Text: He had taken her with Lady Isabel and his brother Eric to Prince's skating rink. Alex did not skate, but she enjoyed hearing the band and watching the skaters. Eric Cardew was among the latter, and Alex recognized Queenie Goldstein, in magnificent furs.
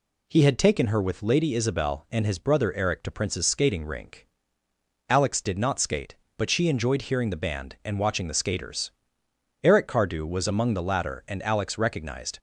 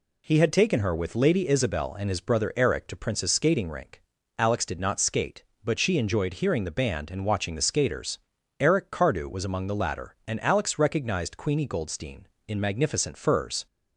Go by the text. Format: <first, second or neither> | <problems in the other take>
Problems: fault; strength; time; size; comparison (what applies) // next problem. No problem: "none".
second | stops before "Queenie Goldstein in magnificent furs"; at 12.3 s